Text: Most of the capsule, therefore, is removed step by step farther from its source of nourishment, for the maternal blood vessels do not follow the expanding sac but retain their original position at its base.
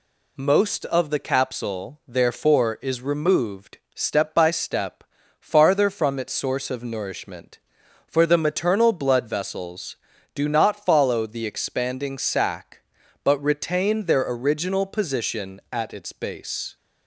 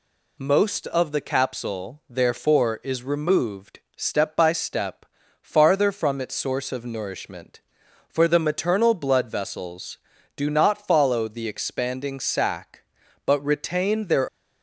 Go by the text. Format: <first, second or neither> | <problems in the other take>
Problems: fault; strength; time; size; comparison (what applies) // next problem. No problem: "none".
first | pauses between "removed" and "step"; slight; at 3.7 s; 0.16 s long; slight in the first // pauses between "step" and "farther"; at 5.0 s; 0.38 s long; also in the first // stops before "original position at its base"; at 14.2 s